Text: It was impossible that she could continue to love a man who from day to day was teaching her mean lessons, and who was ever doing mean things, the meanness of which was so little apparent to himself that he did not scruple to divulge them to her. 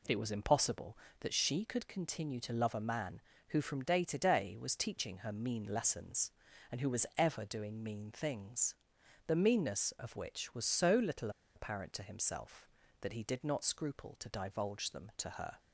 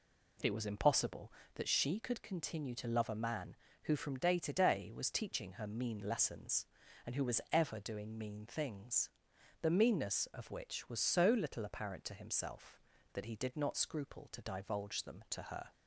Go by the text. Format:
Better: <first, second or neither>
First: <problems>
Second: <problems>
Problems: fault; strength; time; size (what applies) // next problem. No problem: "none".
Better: second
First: pauses between "little" and "apparent"; slight; at 11.2 s; 0.26 s long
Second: none